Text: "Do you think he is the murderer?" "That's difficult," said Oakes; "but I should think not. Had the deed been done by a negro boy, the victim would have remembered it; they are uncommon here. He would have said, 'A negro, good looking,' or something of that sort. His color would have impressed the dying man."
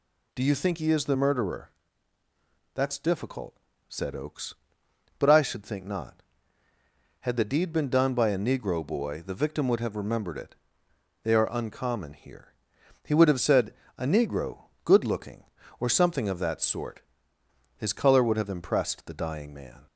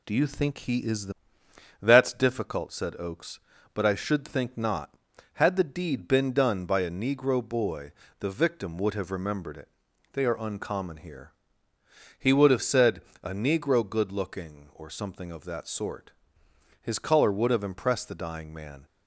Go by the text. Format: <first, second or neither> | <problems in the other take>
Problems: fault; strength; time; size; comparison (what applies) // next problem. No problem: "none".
first | skips "murderer"; at 1.4 s